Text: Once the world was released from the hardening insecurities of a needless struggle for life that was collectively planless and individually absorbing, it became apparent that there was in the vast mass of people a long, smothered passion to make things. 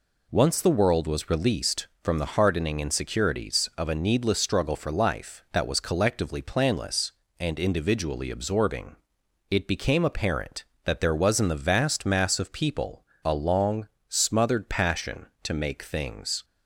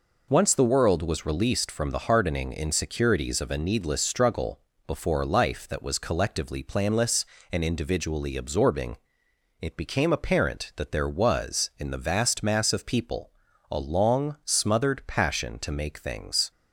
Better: first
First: pauses between "people" and "a"; slight; at 13.0 s; 0.22 s long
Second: says "before" for "for"; at 4.8 s // pauses between "people" and "a"; at 13.3 s; 0.40 s long

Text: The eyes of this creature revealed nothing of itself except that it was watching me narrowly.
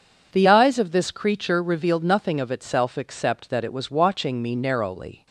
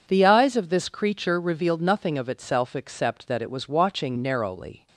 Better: first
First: none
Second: skips "me"; at 4.1 s

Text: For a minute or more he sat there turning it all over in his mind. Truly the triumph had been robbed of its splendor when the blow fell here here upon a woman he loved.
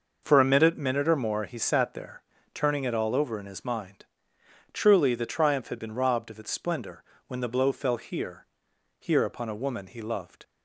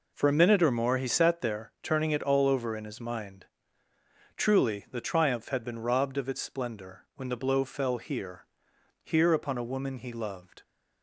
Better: second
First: says "minute" twice; at 0.7 s // pauses between "there" and "turning"; slight; at 2.2 s; 0.32 s long // pauses between "splendor" and "when"; slight; at 7.0 s; 0.26 s long // pauses between "here" and "here"; noticeable; at 8.4 s; 0.52 s long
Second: pauses between "here" and "here"; noticeable; at 8.4 s; 0.60 s long

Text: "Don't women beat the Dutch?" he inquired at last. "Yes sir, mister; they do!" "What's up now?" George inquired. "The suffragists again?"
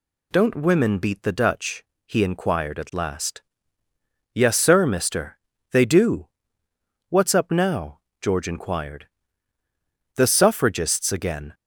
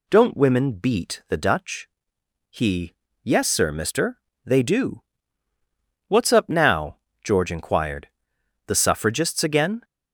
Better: first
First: none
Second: skips "inquired at last"; at 3.0 s

